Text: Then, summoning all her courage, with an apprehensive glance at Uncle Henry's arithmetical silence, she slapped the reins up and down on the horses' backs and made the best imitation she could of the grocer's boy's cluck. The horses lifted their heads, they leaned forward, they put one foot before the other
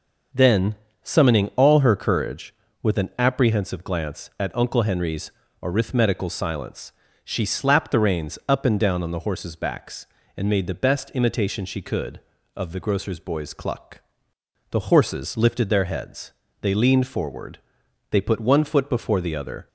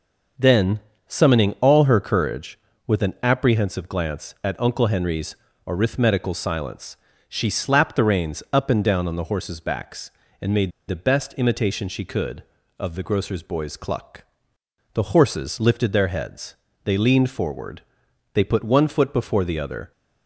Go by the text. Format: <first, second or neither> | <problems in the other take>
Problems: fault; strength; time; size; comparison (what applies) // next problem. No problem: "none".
first | pauses between "Henry's" and "arithmetical"; slight; at 5.3 s; 0.30 s long; slight in the first // pauses between "made" and "the"; slight; at 10.7 s; 0.18 s long